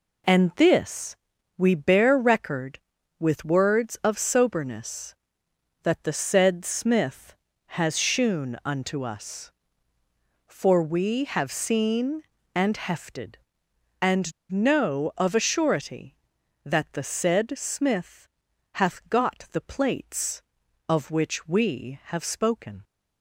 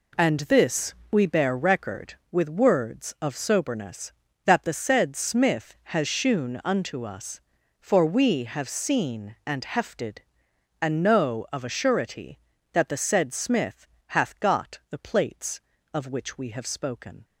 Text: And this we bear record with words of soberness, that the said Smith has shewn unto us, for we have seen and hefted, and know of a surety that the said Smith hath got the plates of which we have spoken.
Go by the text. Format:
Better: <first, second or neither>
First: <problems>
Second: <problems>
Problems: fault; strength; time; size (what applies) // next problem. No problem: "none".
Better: second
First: pauses between "this" and "we"; at 1.1 s; 0.42 s long // pauses between "and" and "know"; slight; at 14.3 s; 0.18 s long // pauses between "Smith" and "hath"; noticeable; at 18.2 s; 0.46 s long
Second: pauses between "this" and "we"; slight; at 0.9 s; 0.18 s long // pauses between "Smith" and "hath"; slight; at 13.8 s; 0.22 s long